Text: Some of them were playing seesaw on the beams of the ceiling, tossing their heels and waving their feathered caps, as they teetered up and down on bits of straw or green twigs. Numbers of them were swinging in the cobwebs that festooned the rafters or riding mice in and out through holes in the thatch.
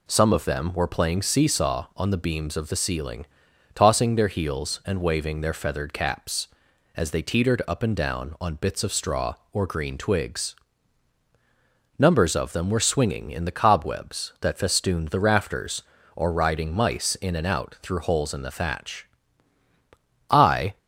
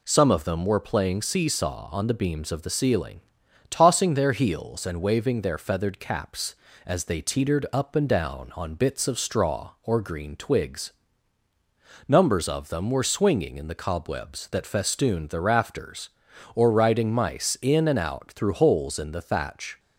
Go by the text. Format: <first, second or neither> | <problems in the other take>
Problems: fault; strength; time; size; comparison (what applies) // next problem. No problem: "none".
second | goes on to say "I"; slight; from 20.2 s on; 0.48 s long